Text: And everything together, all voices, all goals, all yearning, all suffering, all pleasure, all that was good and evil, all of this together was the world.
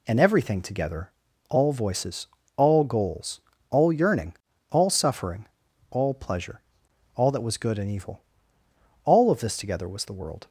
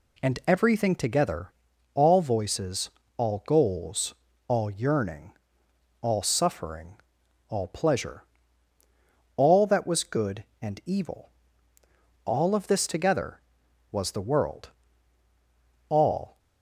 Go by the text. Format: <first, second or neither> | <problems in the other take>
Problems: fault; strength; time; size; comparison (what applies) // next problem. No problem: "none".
first | goes on to say "All"; from 15.8 s on; 0.50 s long